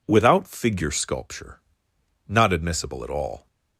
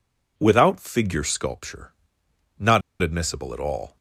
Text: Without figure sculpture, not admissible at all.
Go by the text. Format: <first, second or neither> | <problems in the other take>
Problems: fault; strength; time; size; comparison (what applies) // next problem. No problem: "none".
first | pauses between "not" and "admissible"; slight; at 2.8 s; 0.21 s long